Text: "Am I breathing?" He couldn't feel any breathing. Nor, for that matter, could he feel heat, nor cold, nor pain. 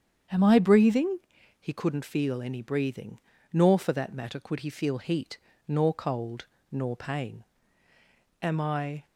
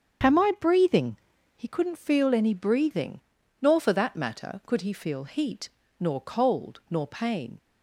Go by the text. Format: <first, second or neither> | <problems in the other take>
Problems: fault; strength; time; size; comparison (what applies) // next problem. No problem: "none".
second | starts louder than the rest; strong; until 1.7 s; 8 dB; strong in the second // goes on to say "Am I"; noticeable; from 8.4 s on; 0.64 s long